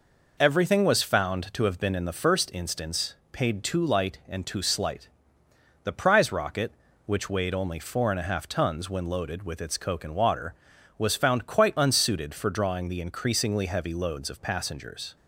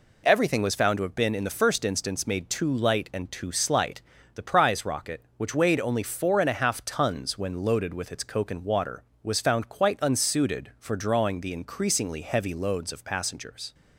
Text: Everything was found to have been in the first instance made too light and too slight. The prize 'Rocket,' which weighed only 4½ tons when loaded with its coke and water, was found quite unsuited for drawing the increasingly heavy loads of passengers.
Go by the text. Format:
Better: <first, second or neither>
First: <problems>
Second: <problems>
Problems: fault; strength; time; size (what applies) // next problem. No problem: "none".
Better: second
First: says "paid" for "made"; at 3.3 s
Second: none